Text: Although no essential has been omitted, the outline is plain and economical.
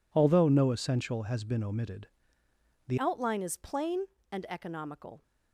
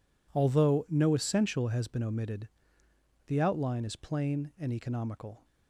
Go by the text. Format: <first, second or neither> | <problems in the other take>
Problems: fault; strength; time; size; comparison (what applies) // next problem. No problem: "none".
second | changes voice at "outline"; from 2.9 s on; 2.3 s long